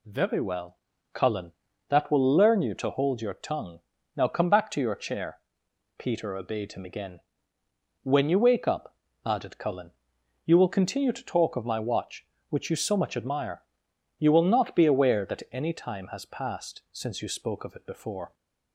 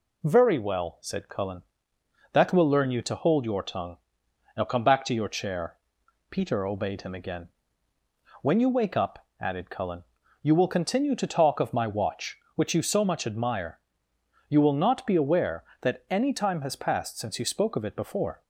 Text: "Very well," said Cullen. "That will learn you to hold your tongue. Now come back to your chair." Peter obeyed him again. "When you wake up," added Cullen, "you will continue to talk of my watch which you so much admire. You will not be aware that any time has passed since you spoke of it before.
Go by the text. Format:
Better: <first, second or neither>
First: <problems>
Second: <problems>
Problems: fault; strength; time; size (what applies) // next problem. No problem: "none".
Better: second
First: skips "said"; at 0.9 s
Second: none